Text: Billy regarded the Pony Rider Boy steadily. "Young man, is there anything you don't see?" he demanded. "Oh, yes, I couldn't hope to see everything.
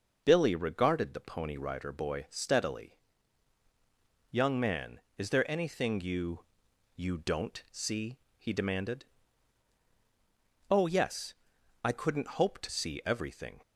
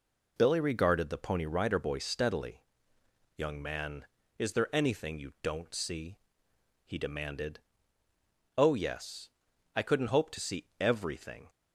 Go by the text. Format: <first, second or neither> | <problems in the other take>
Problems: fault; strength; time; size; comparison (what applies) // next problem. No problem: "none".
second | says "you" twice; at 6.9 s